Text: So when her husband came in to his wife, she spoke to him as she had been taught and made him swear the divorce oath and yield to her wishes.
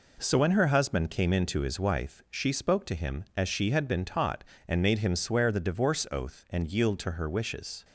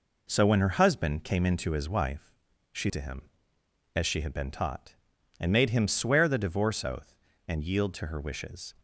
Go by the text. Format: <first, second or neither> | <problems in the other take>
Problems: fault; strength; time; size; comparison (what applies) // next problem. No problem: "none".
first | skips "spoke"; at 2.9 s